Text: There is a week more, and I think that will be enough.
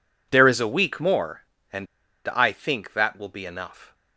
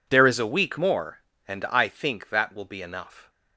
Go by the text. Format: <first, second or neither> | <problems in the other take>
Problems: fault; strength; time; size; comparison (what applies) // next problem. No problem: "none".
second | pauses between "and" and "I"; at 1.8 s; 0.41 s long